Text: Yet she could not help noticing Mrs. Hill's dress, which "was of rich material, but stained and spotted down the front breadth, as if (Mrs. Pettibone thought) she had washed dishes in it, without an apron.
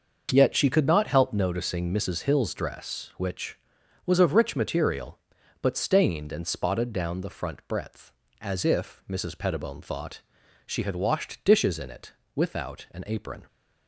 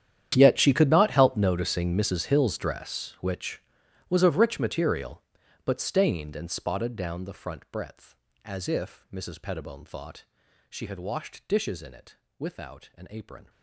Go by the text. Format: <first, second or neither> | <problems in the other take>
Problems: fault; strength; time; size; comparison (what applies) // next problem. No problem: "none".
first | gets quieter; strong; throughout; 20 dB // starts louder than the rest; strong; until 1.3 s; 10 dB; noticeable in the first